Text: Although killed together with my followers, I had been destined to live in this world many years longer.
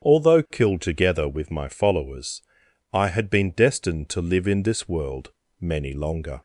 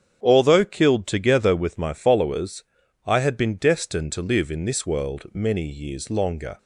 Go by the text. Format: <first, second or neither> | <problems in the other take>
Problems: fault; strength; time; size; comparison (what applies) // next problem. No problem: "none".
second | starts louder than the rest; strong; until 1.1 s; 8.5 dB; strong in the second // pauses between "world" and "many"; slight; at 5.3 s; 0.28 s long // skips "years"; at 5.9 s